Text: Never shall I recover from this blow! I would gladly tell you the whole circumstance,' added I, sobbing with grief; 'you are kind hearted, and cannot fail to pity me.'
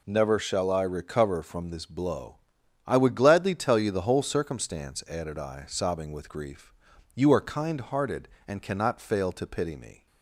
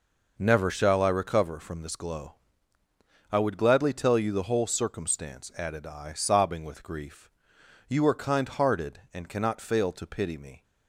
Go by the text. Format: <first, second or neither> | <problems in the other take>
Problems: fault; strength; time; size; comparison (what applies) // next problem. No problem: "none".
first | says "glow" for "blow"; at 1.9 s